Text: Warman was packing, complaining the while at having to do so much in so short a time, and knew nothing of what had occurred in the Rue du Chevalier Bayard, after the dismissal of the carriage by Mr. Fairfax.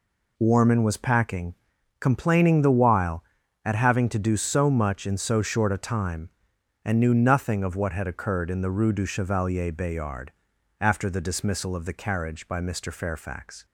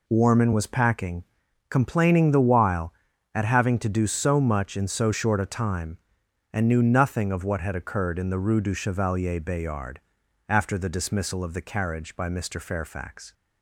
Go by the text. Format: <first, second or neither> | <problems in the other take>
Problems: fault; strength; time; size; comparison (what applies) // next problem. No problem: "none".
neither | none